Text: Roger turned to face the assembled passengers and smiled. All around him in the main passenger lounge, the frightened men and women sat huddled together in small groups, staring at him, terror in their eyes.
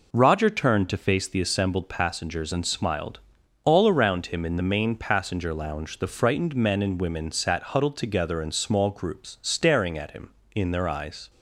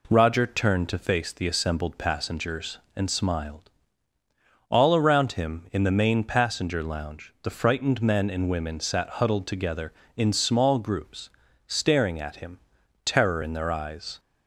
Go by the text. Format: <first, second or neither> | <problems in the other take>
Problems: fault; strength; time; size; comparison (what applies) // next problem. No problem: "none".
second | skips "terror"; at 10.4 s